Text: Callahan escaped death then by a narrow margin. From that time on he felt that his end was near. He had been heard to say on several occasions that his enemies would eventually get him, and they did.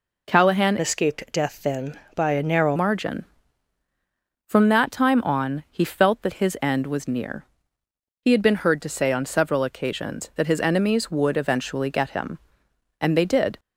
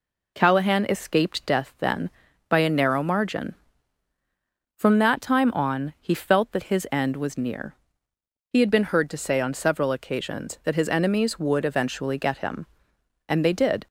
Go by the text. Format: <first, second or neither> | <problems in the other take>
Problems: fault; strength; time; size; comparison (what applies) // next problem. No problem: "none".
second | changes voice from "escaped" to "narrow"; from 0.7 to 2.7 s; 2.0 s long